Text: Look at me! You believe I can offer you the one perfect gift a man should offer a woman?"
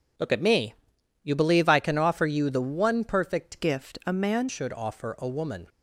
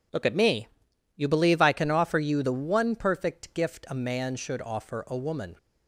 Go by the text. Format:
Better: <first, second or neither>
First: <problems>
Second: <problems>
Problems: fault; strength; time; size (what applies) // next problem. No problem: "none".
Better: second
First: changes voice from "gift" to "man"; from 3.6 to 4.4 s; 0.8 s long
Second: none